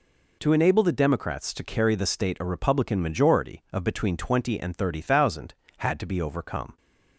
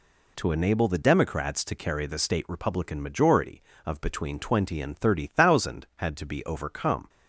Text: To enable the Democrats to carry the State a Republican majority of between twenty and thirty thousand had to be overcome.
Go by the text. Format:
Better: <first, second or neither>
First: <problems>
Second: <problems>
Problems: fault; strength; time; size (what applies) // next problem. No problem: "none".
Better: first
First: none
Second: skips "a"; at 2.4 s